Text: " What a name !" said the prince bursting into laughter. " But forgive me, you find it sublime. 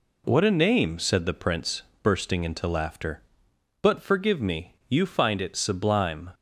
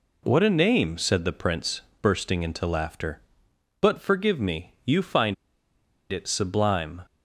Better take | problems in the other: first | pauses between "prince" and "bursting"; slight; at 1.8 s; 0.18 s long; slight in the first // pauses between "find" and "it"; noticeable; at 5.3 s; 0.76 s long

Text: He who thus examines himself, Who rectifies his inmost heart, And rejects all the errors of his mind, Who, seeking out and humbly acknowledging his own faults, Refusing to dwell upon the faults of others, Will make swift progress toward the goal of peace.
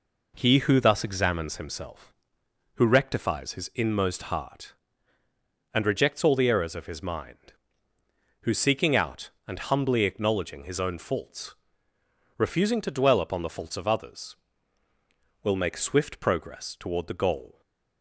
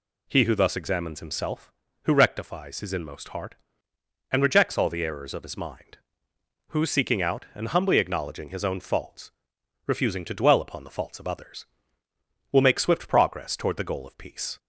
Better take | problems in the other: second | stops before "of peace"; at 17.6 s

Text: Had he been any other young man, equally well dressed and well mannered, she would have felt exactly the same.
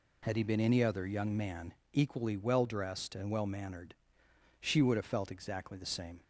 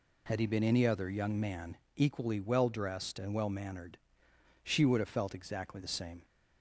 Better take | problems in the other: neither | none

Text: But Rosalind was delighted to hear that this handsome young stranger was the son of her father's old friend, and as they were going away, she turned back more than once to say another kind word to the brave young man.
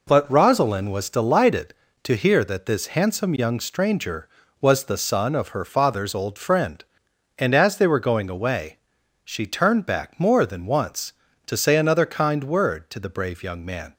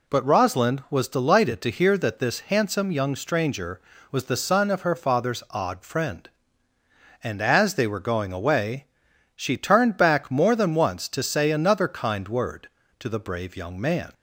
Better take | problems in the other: first | says "odd" for "old"; at 5.5 s

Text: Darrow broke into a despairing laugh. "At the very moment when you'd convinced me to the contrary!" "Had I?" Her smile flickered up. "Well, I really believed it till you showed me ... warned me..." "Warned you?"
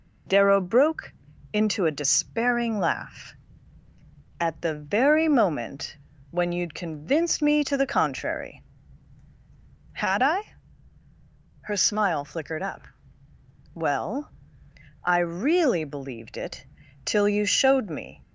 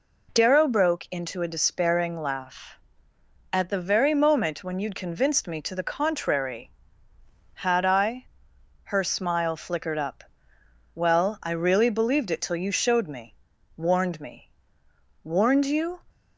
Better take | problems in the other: second | pauses between "broke" and "into"; at 1.1 s; 0.40 s long // pauses between "moment" and "when"; slight; at 5.9 s; 0.36 s long // pauses between "it" and "till"; at 16.6 s; 0.40 s long // stops before "warned me Warned you"; at 18.2 s

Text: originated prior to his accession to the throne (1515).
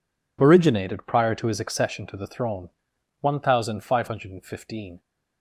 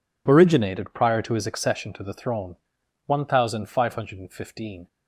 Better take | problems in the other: neither | none

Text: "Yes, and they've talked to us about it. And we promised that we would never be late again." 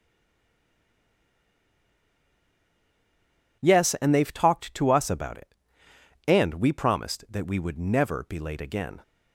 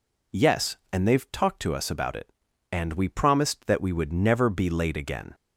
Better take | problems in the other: second | stays silent before the first word; strong; until 3.6 s; 3.6 s long

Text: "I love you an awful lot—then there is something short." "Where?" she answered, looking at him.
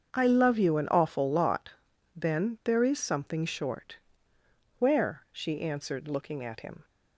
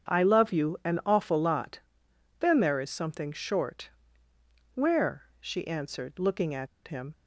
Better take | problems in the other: first | starts louder than the rest; strong; until 1.2 s; 7.5 dB; also in the first // pauses between "at" and "him"; slight; at 6.6 s; 0.19 s long

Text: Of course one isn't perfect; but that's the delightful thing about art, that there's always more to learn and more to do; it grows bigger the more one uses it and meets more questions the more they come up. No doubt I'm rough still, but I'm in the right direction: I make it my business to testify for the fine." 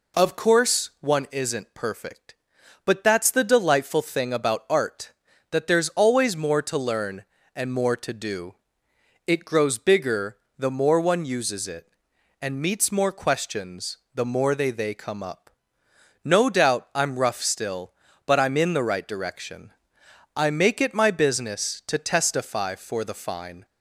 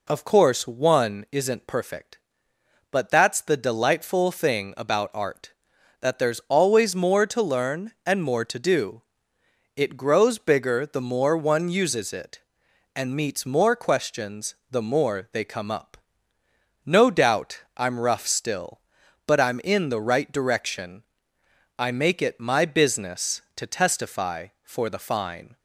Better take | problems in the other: second | pauses between "bigger" and "the"; slight; at 10.3 s; 0.20 s long // pauses between "questions" and "the"; slight; at 13.9 s; 0.16 s long; slight in the second // says "they" twice; at 14.7 s

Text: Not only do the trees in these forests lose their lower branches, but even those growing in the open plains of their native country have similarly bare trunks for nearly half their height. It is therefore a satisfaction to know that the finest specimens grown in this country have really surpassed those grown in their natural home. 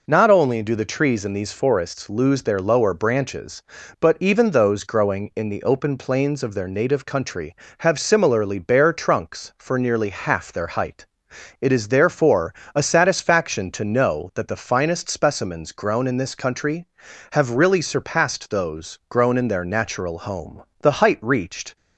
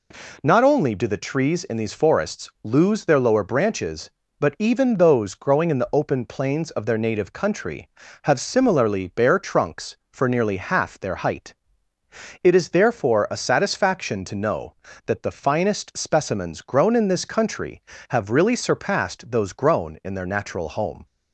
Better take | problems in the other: second | pauses between "therefore" and "a"; slight; at 12.5 s; 0.22 s long // goes on to say "The height reached"; noticeable; from 20.7 s on; 0.96 s long

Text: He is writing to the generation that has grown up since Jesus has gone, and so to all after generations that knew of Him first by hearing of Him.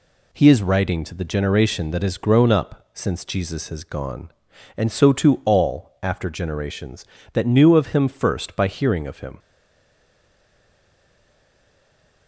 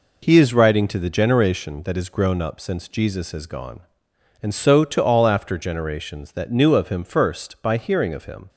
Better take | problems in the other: second | stays silent after the last word; strong; from 9.3 s on; 2.9 s long

